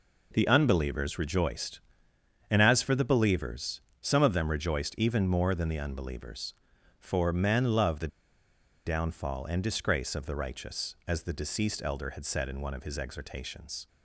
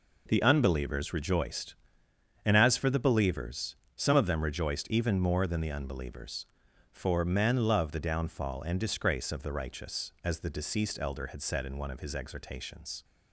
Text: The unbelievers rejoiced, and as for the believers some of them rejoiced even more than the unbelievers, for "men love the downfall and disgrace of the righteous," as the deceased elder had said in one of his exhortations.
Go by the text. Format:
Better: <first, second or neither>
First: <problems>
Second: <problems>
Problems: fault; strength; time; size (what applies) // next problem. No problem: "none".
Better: second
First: pauses between "believers" and "some"; slight; at 3.8 s; 0.18 s long // pauses between "the" and "downfall"; noticeable; at 8.0 s; 0.78 s long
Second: pauses between "believers" and "some"; slight; at 3.7 s; 0.18 s long